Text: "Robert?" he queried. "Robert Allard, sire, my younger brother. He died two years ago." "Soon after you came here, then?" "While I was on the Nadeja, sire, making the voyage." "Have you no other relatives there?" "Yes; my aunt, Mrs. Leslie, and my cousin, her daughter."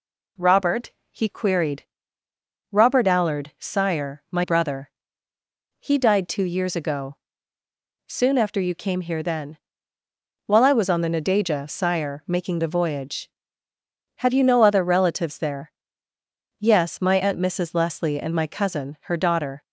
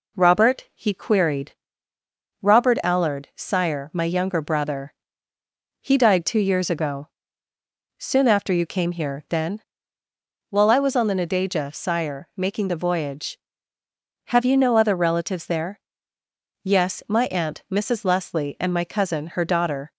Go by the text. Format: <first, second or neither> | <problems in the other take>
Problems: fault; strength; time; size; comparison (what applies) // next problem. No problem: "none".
second | skips "younger"; at 4.4 s